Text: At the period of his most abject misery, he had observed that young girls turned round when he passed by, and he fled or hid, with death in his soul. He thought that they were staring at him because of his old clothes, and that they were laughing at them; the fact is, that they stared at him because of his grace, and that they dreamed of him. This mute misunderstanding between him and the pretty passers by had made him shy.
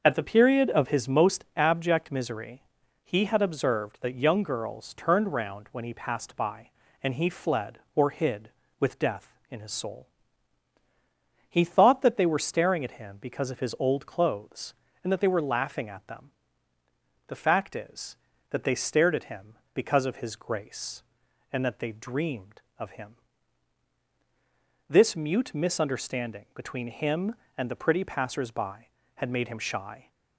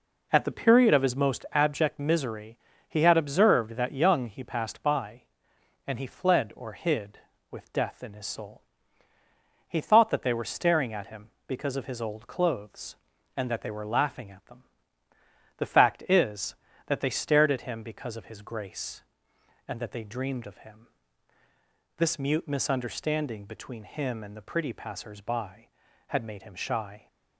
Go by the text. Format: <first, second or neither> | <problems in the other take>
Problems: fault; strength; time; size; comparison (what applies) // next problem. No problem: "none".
first | skips "girls turned round when"; at 4.2 s